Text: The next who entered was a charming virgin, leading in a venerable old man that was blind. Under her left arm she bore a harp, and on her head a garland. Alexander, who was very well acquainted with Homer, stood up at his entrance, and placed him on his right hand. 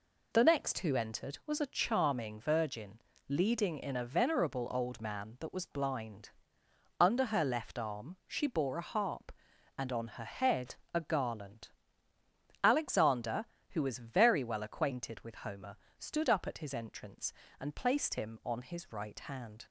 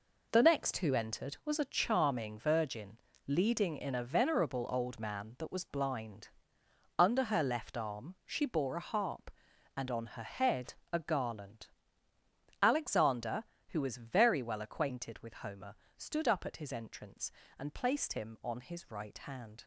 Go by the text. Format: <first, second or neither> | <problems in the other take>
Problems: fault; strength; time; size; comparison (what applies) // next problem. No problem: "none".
first | gets quieter; strong; throughout; 9 dB // pauses between "head" and "a"; slight; at 10.7 s; 0.18 s long; slight in the first